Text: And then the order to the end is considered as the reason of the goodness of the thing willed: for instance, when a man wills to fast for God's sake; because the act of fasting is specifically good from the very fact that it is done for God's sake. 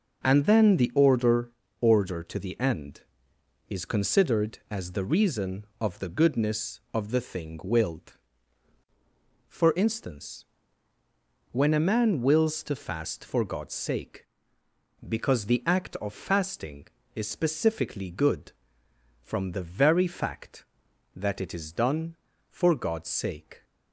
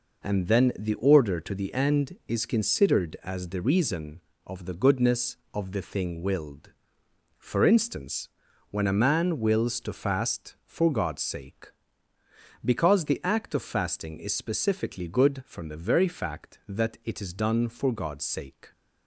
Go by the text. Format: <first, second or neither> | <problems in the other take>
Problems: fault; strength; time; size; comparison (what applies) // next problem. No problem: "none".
second | says "order" twice; at 1.7 s